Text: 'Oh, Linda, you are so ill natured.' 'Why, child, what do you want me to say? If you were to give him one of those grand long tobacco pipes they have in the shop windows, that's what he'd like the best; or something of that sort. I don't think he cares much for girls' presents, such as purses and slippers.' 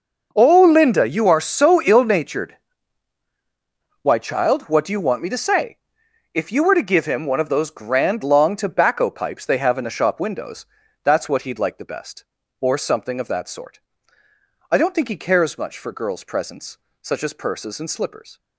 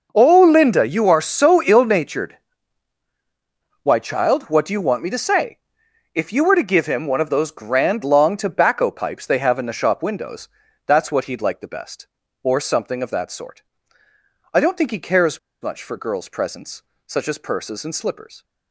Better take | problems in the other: first | pauses between "cares" and "much"; slight; at 15.3 s; 0.22 s long

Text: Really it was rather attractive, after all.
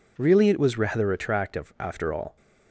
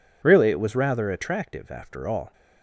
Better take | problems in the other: neither | none

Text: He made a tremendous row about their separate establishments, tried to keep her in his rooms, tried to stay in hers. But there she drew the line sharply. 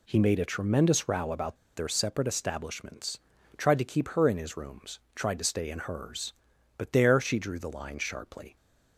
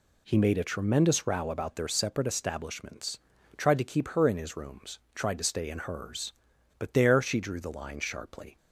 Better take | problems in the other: second | pauses between "about" and "their"; slight; at 1.5 s; 0.19 s long

